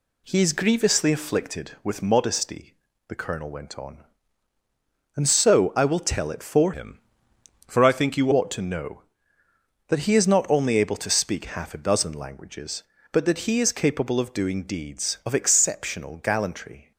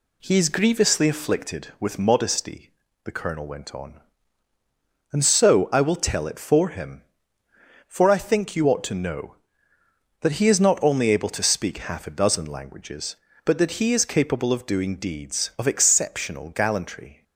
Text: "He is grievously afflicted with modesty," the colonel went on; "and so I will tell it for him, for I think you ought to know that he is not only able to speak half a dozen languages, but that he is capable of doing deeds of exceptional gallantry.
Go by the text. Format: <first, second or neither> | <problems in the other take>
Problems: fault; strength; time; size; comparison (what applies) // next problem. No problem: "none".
second | changes voice from "him" to "you"; from 6.7 to 8.3 s; 1.6 s long